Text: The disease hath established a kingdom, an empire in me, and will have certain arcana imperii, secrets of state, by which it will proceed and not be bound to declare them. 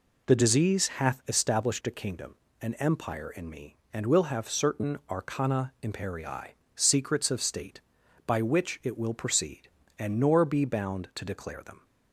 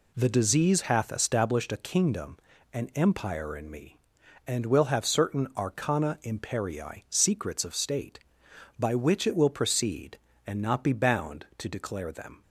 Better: second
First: says "nor" for "not"; at 10.1 s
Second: none

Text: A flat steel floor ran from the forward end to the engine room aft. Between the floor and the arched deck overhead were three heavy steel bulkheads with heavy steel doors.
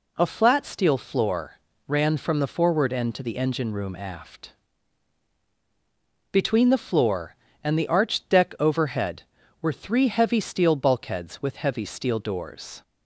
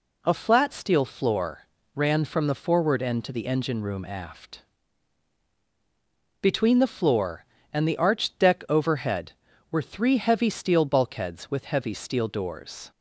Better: neither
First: pauses between "floor" and "ran"; slight; at 1.5 s; 0.30 s long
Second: pauses between "floor" and "ran"; slight; at 1.6 s; 0.30 s long

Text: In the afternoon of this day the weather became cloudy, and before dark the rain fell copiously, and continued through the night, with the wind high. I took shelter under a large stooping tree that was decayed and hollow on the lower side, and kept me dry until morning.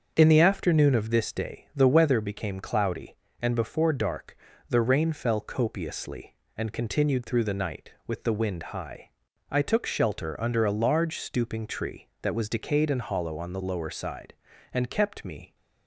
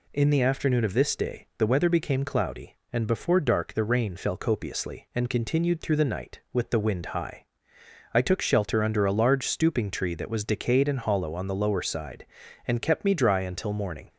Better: second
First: starts louder than the rest; until 1.1 s; 6.5 dB // pauses between "dark" and "the"; slight; at 4.3 s; 0.32 s long // pauses between "wind" and "high"; slight; at 8.6 s; 0.16 s long // stops before "dry until morning"; at 15.5 s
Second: none

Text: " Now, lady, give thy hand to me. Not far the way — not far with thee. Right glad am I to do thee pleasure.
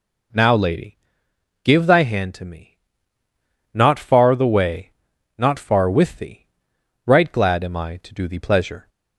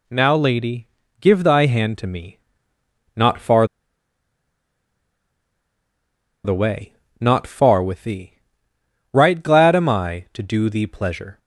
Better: first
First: none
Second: pauses between "far" and "the"; strong; at 3.6 s; 2.7 s long

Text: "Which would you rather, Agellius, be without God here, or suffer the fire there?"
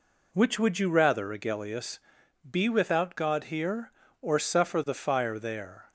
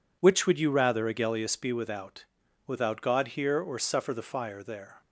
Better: first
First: none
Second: says "without" twice; at 2.6 s

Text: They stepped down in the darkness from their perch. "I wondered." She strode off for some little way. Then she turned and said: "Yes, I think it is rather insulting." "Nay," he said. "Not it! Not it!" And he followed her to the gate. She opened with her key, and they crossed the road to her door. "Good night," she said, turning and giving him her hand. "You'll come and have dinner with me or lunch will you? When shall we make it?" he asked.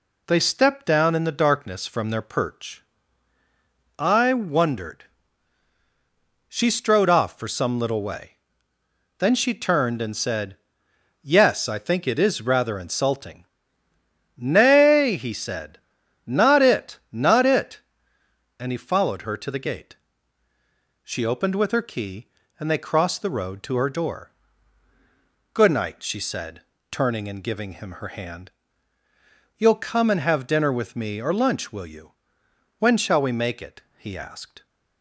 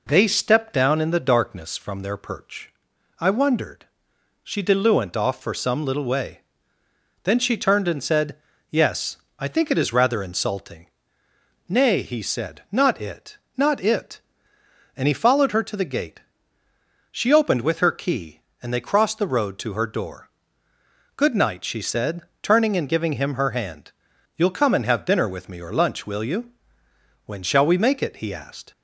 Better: first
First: none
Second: says "diluent" for "strode"; at 4.6 s

